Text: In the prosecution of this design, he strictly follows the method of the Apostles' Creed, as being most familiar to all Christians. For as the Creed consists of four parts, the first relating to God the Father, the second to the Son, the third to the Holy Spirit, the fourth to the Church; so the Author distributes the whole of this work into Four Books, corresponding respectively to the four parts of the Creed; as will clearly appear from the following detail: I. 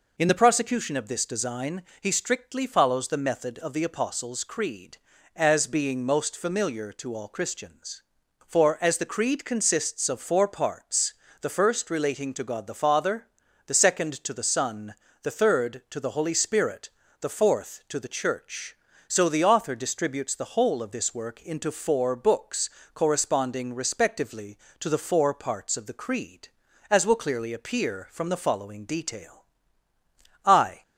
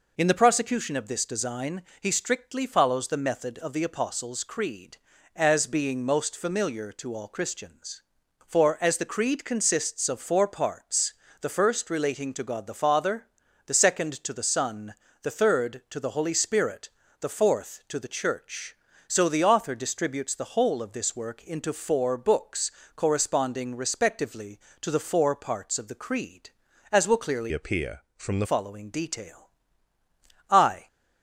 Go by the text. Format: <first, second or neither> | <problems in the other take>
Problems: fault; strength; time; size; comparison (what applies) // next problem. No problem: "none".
first | changes voice from "appear" to "the"; from 27.5 to 28.4 s; 0.9 s long